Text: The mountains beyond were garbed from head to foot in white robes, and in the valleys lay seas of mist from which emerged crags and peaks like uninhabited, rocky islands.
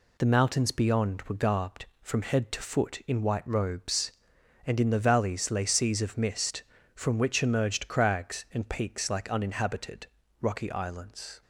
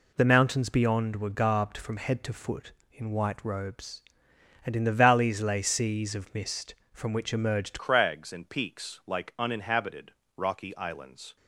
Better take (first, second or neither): first